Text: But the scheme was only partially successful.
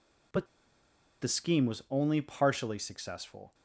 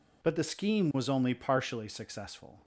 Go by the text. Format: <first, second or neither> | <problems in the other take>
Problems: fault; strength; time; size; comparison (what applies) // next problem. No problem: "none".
second | pauses between "But" and "the"; noticeable; at 0.4 s; 0.76 s long